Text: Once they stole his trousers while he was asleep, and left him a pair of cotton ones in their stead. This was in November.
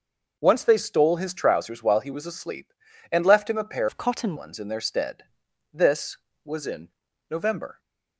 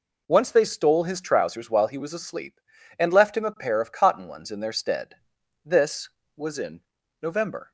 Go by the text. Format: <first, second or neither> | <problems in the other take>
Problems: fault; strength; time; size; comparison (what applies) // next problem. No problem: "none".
second | changes voice from "of" to "cotton"; from 3.8 to 4.3 s; 0.5 s long // pauses between "in" and "November"; at 6.8 s; 0.40 s long; also in the second